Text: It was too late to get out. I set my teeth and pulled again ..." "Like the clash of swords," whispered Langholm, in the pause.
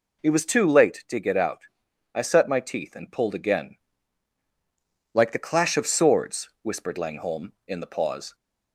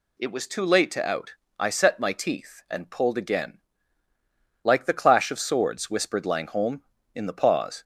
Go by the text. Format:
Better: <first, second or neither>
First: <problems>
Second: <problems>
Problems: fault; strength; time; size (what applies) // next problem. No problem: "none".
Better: first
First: none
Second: skips "get"; at 1.0 s